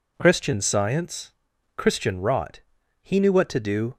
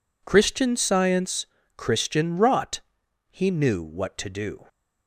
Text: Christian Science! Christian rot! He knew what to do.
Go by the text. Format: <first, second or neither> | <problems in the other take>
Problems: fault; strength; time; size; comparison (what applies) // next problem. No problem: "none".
neither | none